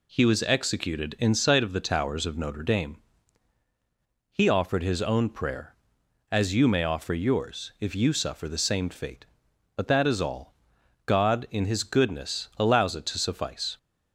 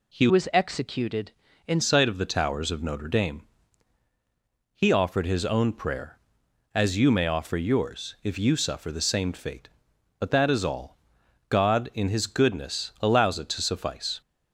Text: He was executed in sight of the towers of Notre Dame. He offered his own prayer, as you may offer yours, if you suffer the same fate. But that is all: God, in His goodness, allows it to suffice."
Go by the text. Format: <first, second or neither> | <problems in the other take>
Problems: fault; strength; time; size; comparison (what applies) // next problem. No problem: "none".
first | changes voice from "was" to "in"; from 0.2 to 1.8 s; 1.6 s long